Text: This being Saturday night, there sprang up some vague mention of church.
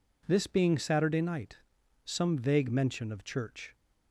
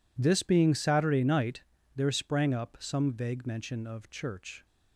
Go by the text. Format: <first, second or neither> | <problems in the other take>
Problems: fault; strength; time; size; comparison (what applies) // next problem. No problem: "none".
second | skips "there sprang up"; at 1.8 s